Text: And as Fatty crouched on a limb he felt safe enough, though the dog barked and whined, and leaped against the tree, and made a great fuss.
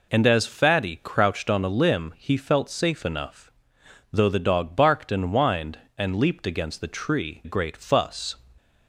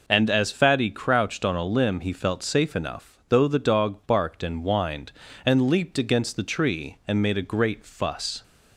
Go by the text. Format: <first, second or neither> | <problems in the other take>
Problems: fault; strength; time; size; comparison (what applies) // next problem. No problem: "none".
second | skips "and made a"; at 7.4 s